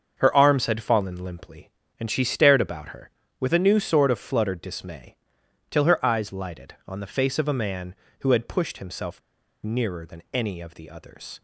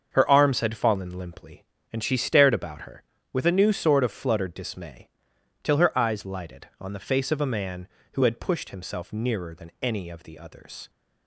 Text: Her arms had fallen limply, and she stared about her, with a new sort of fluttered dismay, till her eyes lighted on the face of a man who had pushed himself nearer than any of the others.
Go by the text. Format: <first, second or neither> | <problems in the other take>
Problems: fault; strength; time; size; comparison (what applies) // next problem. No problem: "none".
second | starts louder than the rest; until 1.1 s; 6.5 dB; also in the second // pauses between "himself" and "nearer"; at 9.1 s; 0.43 s long